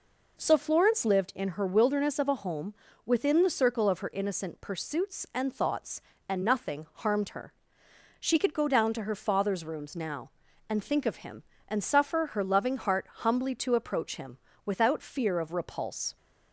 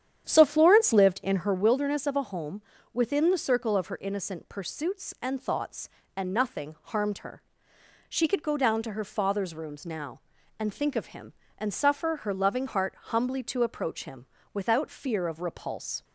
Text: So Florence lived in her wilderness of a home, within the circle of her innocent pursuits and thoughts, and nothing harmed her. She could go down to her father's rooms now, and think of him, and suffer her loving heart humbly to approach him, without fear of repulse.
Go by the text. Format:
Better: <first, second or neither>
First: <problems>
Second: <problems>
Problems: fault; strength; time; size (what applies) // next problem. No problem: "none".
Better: first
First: none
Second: starts louder than the rest; strong; until 1.7 s; 9.5 dB